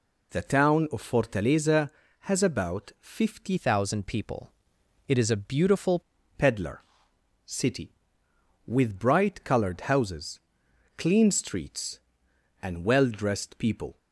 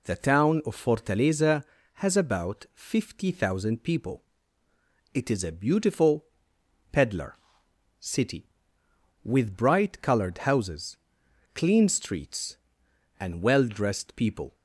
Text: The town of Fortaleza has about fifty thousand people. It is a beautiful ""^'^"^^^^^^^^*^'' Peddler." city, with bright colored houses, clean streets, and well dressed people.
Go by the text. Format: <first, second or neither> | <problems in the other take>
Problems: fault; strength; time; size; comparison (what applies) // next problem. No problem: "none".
second | changes voice from "thousand" to "beautiful"; from 3.5 to 5.9 s; 2.4 s long